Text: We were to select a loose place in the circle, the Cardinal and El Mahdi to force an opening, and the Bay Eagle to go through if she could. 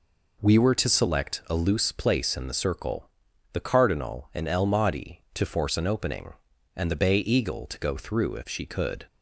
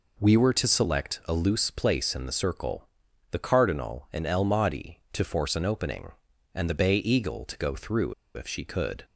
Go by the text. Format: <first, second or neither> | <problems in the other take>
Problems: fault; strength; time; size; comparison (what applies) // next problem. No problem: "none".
first | pauses between "through" and "if"; slight; at 8.1 s; 0.23 s long